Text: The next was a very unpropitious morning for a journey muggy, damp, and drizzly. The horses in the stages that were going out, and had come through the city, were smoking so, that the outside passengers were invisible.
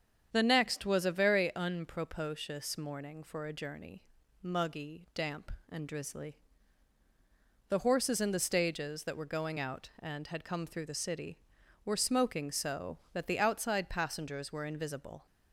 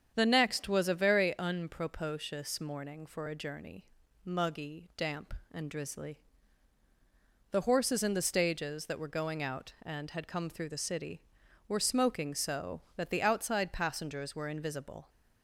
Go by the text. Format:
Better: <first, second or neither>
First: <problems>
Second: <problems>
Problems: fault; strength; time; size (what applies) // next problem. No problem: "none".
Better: neither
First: starts louder than the rest; strong; until 1.3 s; 8 dB // pauses between "journey" and "muggy"; at 4.0 s; 0.40 s long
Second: starts louder than the rest; strong; until 1.1 s; 8 dB // pauses between "journey" and "muggy"; at 3.8 s; 0.40 s long